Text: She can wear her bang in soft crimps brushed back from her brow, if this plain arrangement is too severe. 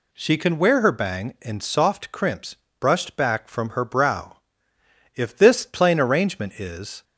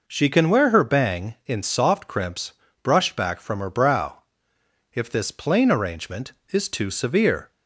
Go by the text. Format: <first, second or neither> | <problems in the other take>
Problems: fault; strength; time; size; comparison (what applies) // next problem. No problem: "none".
second | pauses between "crimps" and "brushed"; slight; at 2.5 s; 0.24 s long; slight in the second // stops before "too severe"; at 7.0 s